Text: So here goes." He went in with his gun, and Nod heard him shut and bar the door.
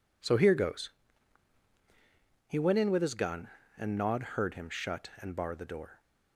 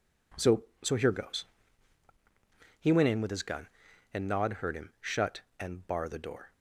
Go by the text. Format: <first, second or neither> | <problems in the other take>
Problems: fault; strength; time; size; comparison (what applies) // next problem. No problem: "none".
first | says "So" twice; at 0.8 s